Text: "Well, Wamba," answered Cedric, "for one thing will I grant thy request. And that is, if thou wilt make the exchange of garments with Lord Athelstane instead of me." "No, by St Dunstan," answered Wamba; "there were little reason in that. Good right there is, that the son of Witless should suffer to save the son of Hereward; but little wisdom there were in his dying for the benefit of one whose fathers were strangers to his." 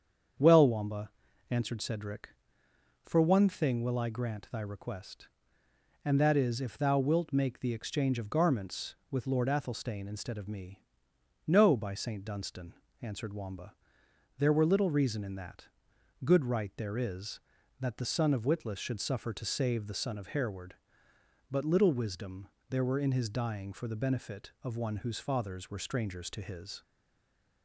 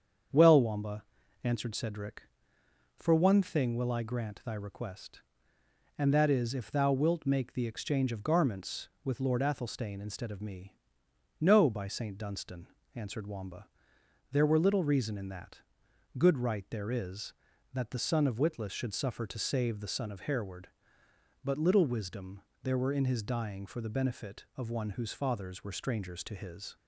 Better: second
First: starts louder than the rest; strong; until 1.7 s; 7.5 dB // pauses between "wisdom" and "there"; slight; at 22.4 s; 0.20 s long // stays silent after the last word; slight; from 26.8 s on; 0.8 s long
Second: starts louder than the rest; strong; until 1.7 s; 7.5 dB // pauses between "wisdom" and "there"; slight; at 22.4 s; 0.20 s long

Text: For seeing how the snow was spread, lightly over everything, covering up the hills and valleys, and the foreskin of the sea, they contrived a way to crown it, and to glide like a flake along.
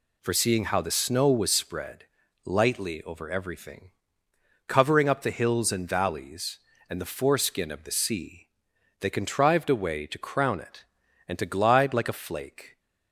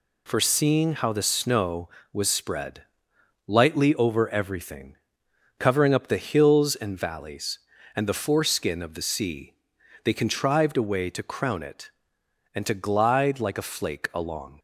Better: second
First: stops before "along"; at 12.7 s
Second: none

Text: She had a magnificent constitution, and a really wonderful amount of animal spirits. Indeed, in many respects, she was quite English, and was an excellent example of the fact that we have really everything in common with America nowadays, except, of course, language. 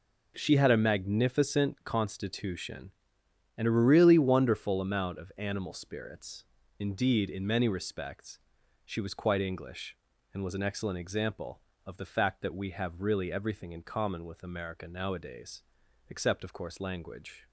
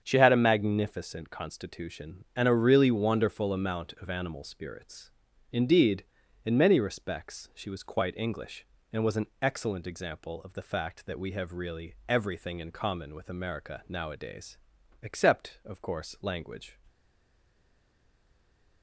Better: first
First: none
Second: starts louder than the rest; strong; until 1.0 s; 7.5 dB // stays silent after the last word; noticeable; from 16.8 s on; 2.0 s long

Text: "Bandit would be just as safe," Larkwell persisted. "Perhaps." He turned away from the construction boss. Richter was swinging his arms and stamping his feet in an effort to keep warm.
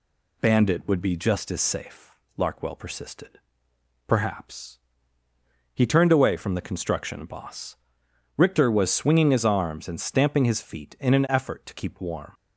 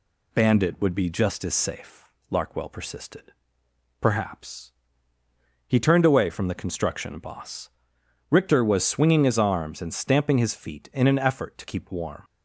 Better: neither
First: none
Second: none

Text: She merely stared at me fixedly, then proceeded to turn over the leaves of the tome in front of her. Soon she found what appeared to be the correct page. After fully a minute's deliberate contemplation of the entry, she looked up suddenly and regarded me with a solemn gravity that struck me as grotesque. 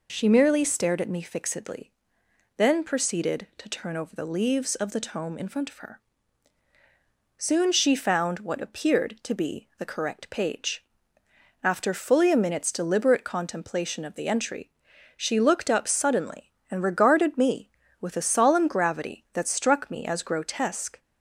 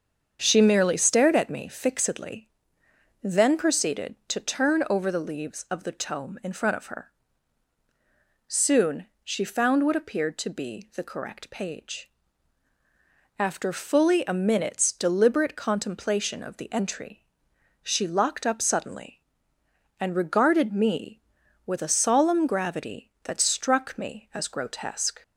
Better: first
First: none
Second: starts louder than the rest; strong; until 1.4 s; 7 dB // pauses between "Soon" and "she"; slight; at 9.0 s; 0.18 s long // says "locked" for "looked"; at 18.0 s

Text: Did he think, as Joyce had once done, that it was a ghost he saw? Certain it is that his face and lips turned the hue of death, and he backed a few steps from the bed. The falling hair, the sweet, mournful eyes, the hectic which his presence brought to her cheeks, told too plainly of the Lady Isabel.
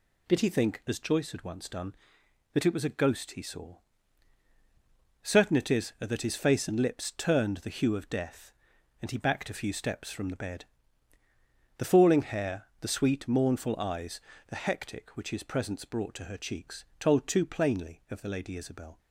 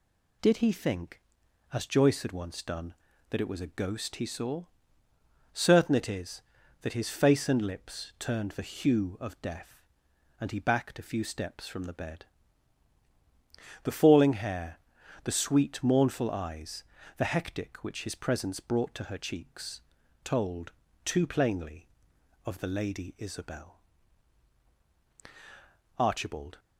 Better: first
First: none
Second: pauses between "told" and "too"; slight; at 20.7 s; 0.32 s long // goes on to say "Archibald"; noticeable; from 25.9 s on; 0.62 s long

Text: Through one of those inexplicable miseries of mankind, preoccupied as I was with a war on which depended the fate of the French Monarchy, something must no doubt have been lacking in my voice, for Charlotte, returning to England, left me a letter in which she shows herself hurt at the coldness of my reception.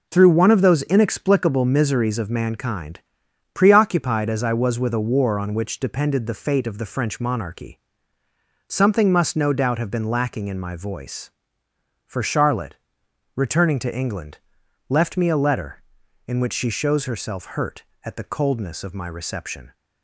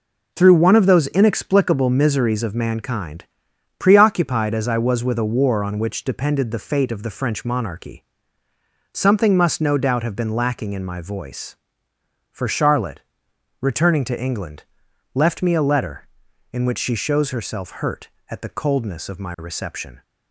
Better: neither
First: none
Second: none

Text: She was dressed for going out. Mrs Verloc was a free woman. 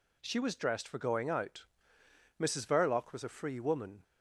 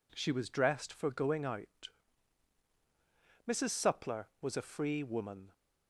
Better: first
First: none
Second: says "Suppler" for "Verloc"; at 3.7 s

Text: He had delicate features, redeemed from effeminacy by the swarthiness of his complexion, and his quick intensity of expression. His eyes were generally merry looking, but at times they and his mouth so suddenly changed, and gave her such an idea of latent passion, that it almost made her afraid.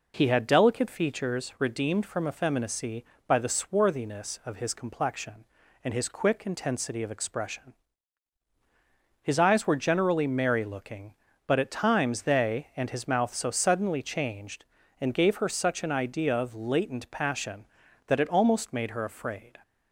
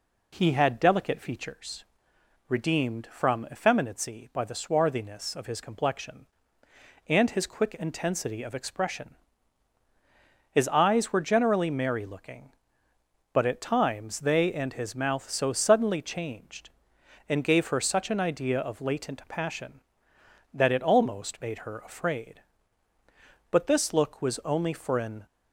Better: first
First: none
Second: goes on to say "But this look was only for an"; strong; from 23.5 s on; 1.7 s long

